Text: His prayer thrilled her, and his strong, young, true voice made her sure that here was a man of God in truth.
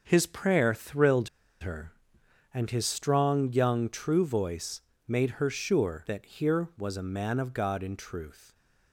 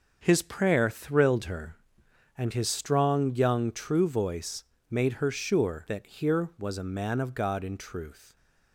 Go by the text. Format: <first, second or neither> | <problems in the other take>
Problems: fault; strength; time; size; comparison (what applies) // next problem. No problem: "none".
second | pauses between "thrilled" and "her"; slight; at 1.2 s; 0.33 s long // pauses between "voice" and "made"; slight; at 4.8 s; 0.28 s long; slight in the second